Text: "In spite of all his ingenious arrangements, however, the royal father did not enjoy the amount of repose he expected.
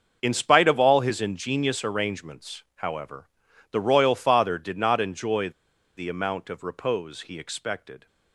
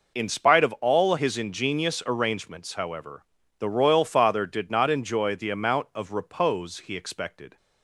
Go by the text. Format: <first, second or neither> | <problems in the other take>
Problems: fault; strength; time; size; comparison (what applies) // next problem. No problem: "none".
second | starts louder than the rest; until 1.2 s; 6.5 dB // pauses between "enjoy" and "the"; noticeable; at 5.4 s; 0.46 s long